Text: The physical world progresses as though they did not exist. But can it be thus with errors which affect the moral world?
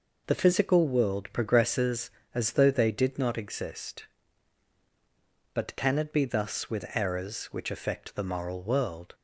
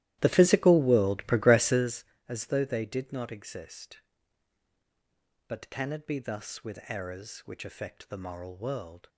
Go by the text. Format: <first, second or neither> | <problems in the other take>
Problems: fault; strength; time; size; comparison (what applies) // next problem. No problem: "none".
first | starts louder than the rest; strong; until 2.1 s; 14 dB